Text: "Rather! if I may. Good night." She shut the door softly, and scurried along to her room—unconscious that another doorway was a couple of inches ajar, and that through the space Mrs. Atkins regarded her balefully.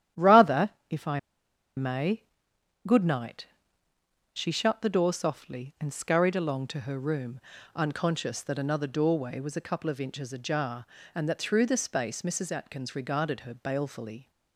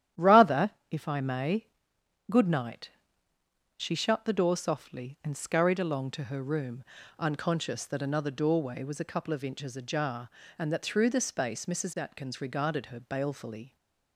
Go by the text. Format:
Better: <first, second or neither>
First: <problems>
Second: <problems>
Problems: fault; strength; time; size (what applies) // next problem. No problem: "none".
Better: second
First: starts louder than the rest; strong; until 1.9 s; 11 dB // pauses between "I" and "may"; noticeable; at 1.1 s; 0.57 s long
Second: starts louder than the rest; strong; until 1.3 s; 11 dB